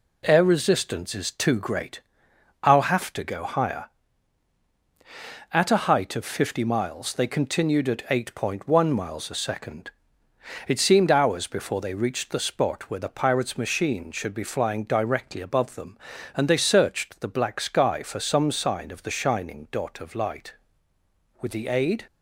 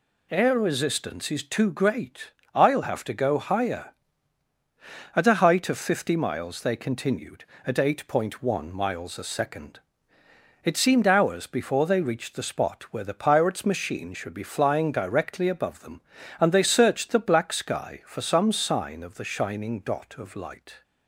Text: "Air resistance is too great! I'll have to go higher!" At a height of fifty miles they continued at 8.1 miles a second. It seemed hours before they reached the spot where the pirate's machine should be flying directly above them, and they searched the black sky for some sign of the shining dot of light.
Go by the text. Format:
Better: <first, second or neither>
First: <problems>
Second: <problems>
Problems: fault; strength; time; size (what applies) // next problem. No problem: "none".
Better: second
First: goes on to say "With the aid"; noticeable; from 21.4 s on; 0.64 s long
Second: none